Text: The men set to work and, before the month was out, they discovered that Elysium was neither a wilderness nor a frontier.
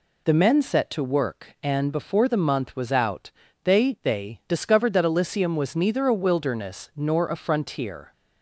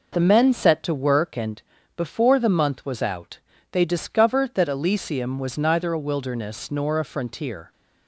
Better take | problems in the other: second | says "they" twice; at 4.0 s

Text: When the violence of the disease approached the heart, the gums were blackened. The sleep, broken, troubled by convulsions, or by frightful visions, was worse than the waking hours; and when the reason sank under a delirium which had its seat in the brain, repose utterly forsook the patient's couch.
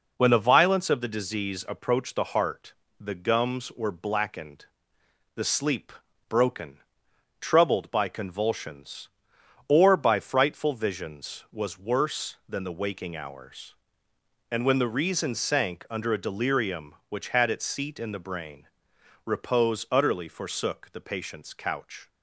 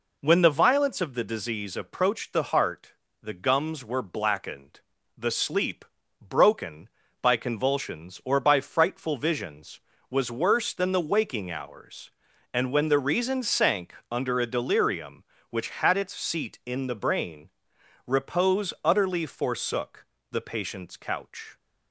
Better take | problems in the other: first | skips "troubled"; at 7.0 s // pauses between "sank" and "under"; slight; at 13.9 s; 0.16 s long // pauses between "forsook" and "the"; slight; at 20.0 s; 0.28 s long

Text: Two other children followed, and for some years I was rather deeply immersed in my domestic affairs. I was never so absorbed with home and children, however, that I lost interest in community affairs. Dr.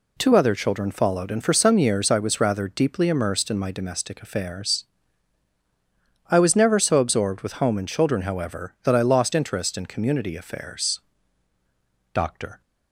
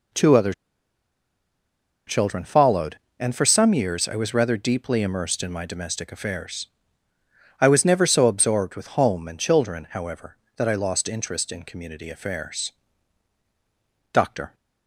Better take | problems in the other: first | pauses between "other" and "children"; strong; at 0.5 s; 1.5 s long

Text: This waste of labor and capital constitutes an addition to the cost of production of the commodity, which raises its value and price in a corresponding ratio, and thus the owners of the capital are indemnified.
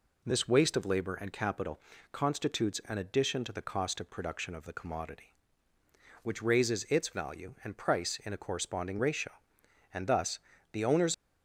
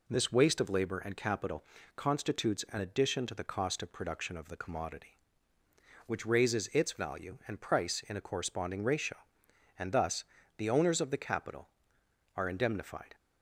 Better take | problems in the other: second | pauses between "capital" and "constitutes"; slight; at 1.8 s; 0.32 s long; slight in the second // pauses between "thus" and "the"; slight; at 10.3 s; 0.34 s long; slight in the second // stops before "of the capital are indemnified"; at 11.1 s

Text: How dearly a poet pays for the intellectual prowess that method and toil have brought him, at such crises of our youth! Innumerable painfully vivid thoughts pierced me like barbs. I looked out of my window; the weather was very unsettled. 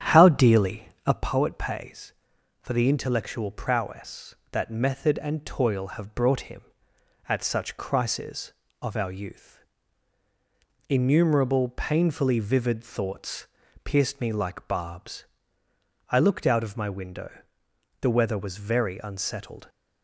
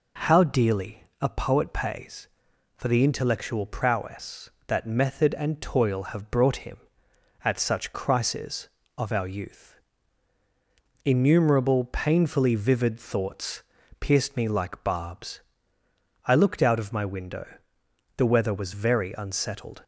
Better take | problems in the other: second | starts louder than the rest; strong; until 1.3 s; 9 dB // pauses between "dearly" and "a"; slight; at 0.8 s; 0.16 s long; slight in the second // pauses between "thoughts" and "pierced"; at 13.4 s; 0.38 s long; also in the second

